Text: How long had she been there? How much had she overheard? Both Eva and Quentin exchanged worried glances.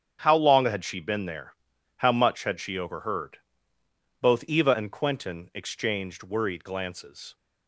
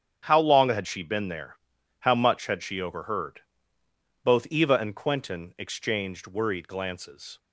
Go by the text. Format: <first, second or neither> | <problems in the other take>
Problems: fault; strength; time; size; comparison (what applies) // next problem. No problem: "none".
neither | starts louder than the rest; strong; the same in both